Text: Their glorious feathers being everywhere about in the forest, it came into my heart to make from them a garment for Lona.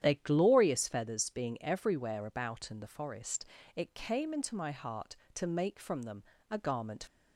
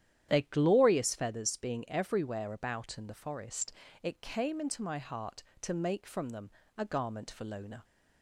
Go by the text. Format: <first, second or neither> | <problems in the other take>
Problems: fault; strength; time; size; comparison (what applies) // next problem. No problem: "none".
second | starts louder than the rest; strong; until 1.1 s; 10 dB; strong in the second // pauses between "them" and "a"; slight; at 6.2 s; 0.26 s long; slight in the second // stops before "for Lona"; at 7.0 s